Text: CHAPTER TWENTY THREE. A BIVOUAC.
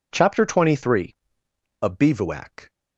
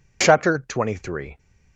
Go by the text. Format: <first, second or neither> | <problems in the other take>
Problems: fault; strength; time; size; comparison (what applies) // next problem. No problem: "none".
first | stops before "A BIVOUAC"; at 1.3 s